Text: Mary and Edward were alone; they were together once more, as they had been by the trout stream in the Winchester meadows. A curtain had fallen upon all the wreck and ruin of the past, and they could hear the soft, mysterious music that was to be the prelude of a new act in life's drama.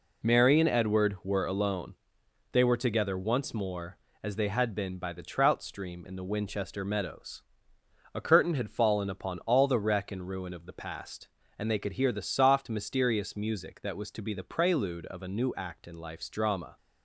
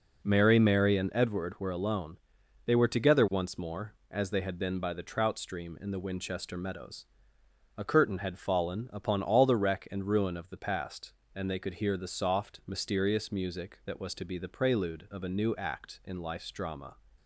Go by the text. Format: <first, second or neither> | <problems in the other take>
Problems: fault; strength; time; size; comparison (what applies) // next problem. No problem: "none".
first | says "Mary" twice; at 0.5 s